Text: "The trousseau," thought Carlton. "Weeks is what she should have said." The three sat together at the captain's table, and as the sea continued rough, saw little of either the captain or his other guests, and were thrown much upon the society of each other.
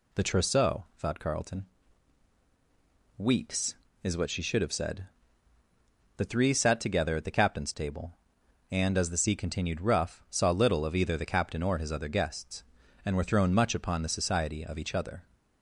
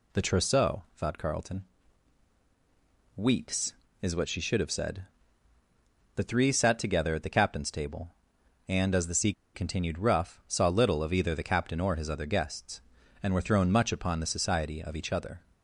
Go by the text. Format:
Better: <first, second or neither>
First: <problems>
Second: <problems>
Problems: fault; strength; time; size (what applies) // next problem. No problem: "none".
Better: first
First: none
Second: pauses between "sea" and "continued"; slight; at 9.3 s; 0.22 s long